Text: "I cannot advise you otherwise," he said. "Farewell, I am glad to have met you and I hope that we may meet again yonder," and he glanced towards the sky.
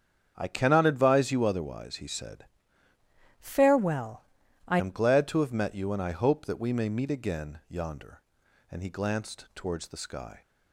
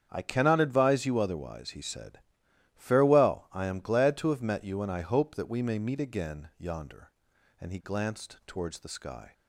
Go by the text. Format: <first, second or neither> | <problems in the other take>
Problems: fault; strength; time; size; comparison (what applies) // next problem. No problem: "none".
second | starts louder than the rest; strong; until 1.3 s; 8 dB; strong in the second // changes voice from "Farewell" to "I"; from 3.3 to 4.7 s; 1.4 s long